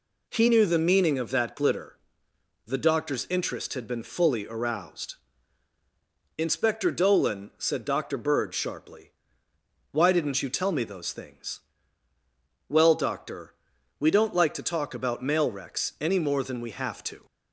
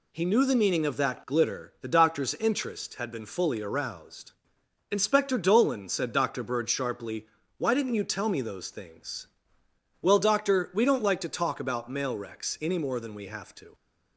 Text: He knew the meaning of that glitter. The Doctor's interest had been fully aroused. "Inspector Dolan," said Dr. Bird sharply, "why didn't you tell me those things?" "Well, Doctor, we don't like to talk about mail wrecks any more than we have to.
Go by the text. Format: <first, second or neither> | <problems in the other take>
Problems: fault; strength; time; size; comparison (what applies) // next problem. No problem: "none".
neither | none